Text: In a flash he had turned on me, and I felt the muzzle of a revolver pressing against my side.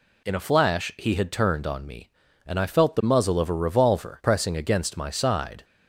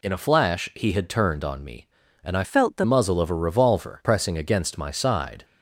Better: first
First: none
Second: changes voice from "felt" to "the"; from 2.4 to 2.8 s; 0.4 s long

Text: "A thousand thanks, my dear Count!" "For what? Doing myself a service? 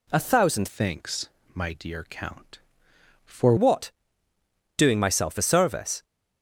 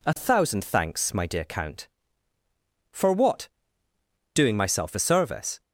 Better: second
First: changes voice from "thanks" to "For"; from 0.6 to 3.5 s; 2.9 s long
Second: none

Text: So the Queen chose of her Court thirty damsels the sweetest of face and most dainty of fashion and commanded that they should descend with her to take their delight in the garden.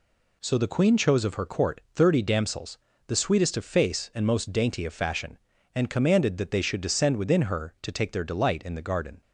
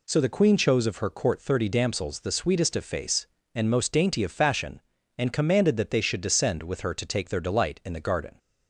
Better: second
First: pauses between "damsels" and "the"; slight; at 2.7 s; 0.30 s long // says "within" for "with"; at 7.1 s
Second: none

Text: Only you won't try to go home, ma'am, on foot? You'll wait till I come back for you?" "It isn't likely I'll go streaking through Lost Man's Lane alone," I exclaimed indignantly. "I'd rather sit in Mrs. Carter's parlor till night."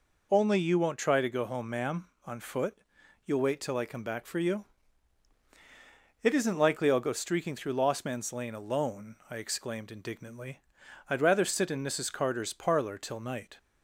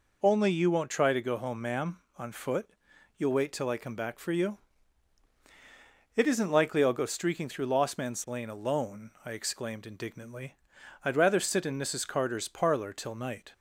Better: neither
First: none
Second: none

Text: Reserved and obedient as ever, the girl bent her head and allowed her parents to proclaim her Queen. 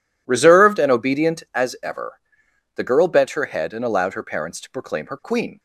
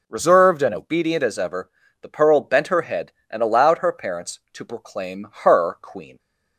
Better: first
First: none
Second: says "pearl" for "girl"; at 2.1 s // pauses between "proclaim" and "her"; slight; at 5.2 s; 0.16 s long

